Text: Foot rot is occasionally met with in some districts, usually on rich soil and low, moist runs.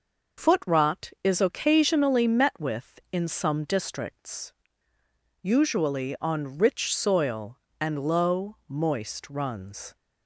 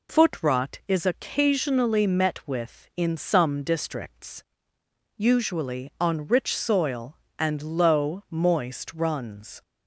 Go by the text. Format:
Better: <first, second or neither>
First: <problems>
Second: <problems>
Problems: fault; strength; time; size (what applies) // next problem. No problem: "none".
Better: neither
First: none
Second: none